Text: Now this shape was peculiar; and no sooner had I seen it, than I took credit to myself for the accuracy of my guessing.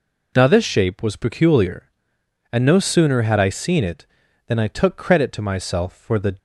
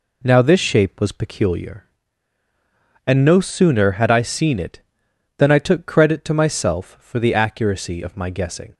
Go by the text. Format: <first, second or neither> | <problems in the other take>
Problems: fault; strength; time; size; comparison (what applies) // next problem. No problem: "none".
second | stops before "accuracy of my guessing"; at 6.3 s